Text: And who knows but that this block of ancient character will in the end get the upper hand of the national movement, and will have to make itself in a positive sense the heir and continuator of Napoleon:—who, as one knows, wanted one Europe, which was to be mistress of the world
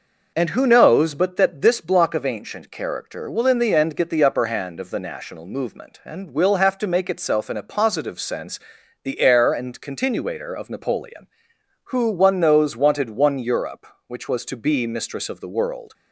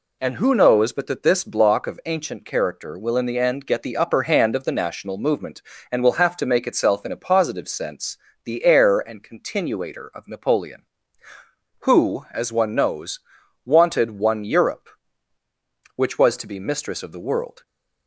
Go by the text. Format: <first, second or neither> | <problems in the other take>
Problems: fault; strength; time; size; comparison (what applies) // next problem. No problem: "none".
second | pauses between "sense" and "the"; at 8.5 s; 0.44 s long; slight in the second // skips "as"; at 12.0 s